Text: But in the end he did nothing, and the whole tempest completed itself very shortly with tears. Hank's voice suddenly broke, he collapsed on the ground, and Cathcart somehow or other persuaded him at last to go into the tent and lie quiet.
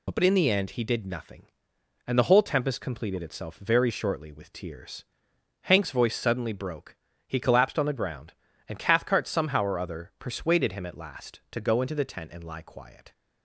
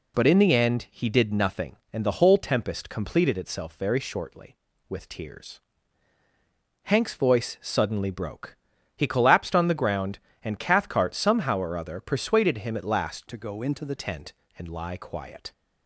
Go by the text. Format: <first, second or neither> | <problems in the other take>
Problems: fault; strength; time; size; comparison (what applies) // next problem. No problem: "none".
first | changes voice from "to" to "the"; from 13.2 to 13.9 s; 0.7 s long